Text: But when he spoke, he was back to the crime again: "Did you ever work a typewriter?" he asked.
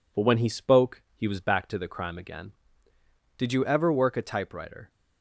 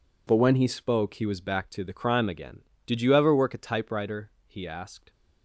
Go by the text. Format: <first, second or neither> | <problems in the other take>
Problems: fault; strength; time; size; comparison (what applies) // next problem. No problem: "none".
second | stops before "he asked"; at 4.8 s